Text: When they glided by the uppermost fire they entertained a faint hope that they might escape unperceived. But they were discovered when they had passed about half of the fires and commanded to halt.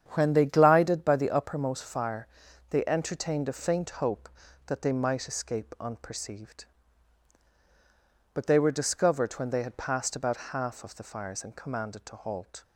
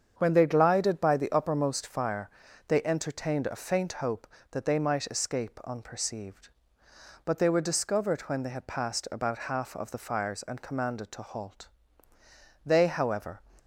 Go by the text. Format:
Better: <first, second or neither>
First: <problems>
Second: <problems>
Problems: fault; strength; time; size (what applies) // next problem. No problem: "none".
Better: first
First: starts louder than the rest; strong; until 1.1 s; 8.5 dB // pauses between "fire" and "they"; at 2.2 s; 0.42 s long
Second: starts louder than the rest; strong; until 1.1 s; 7.5 dB // pauses between "fire" and "they"; at 2.2 s; 0.38 s long // goes on to say "They however"; noticeable; from 12.6 s on; 0.76 s long